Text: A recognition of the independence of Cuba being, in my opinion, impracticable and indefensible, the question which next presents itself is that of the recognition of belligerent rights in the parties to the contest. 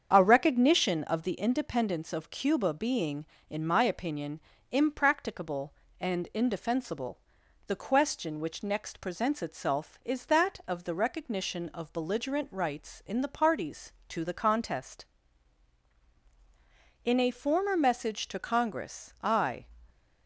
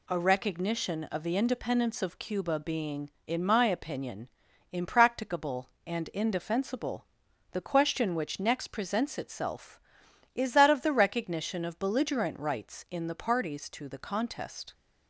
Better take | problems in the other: second | starts louder than the rest; strong; until 1.1 s; 7.5 dB // goes on to say "In a former message to Congress I"; strong; from 17.0 s on; 2.5 s long

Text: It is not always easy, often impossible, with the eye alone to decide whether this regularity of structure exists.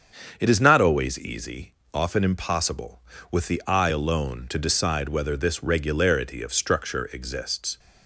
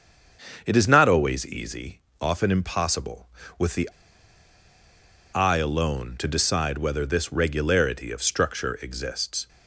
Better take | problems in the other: first | starts louder than the rest; strong; until 1.6 s; 7 dB; strong in the first // pauses between "the" and "eye"; strong; at 3.8 s; 1.4 s long

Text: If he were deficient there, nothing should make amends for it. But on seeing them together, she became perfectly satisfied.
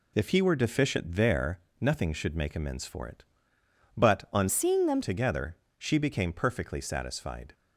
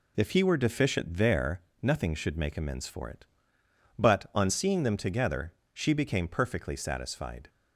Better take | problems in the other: second | changes voice from "seeing" to "them"; from 4.4 to 5.0 s; 0.6 s long

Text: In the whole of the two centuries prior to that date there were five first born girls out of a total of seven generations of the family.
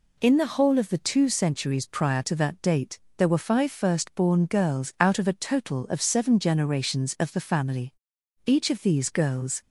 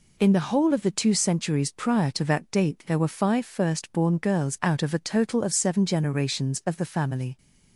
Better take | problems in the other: second | pauses between "date" and "there"; slight; at 2.9 s; 0.20 s long // goes on to say "Each of these girls"; noticeable; from 8.4 s on; 1.1 s long

